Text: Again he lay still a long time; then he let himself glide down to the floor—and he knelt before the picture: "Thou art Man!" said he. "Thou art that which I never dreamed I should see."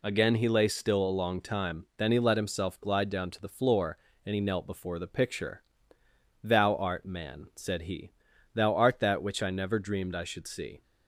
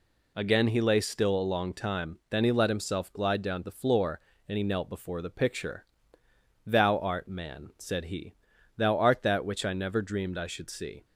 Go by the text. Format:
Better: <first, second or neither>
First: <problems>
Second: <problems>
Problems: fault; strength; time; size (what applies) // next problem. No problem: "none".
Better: first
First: none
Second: skips "to"; at 3.6 s